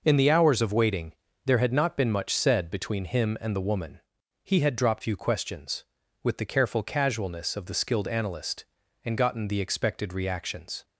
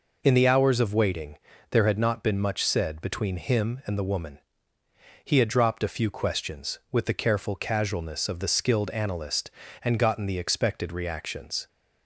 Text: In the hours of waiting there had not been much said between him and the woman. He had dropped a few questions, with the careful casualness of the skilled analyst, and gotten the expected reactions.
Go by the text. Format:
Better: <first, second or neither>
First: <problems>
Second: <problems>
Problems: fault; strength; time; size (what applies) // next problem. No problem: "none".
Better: second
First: pauses between "waiting" and "there"; slight; at 1.1 s; 0.32 s long // skips "a"; at 5.0 s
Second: pauses between "waiting" and "there"; slight; at 1.3 s; 0.32 s long